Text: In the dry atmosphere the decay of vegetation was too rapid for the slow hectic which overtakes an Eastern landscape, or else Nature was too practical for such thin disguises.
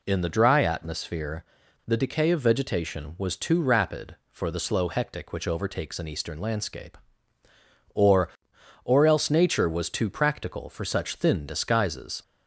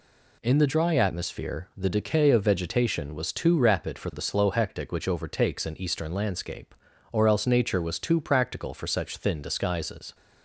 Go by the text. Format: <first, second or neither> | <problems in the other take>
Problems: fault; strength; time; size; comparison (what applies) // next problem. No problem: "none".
second | pauses between "atmosphere" and "the"; at 1.4 s; 0.43 s long // says "or" twice; at 8.8 s